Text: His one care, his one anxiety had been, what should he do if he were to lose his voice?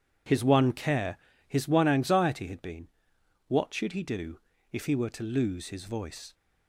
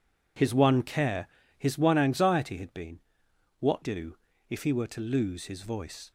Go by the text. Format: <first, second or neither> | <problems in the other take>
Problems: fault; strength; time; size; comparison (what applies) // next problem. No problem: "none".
first | skips "should he"; at 3.8 s // pauses between "do" and "if"; slight; at 4.1 s; 0.32 s long; slight in the first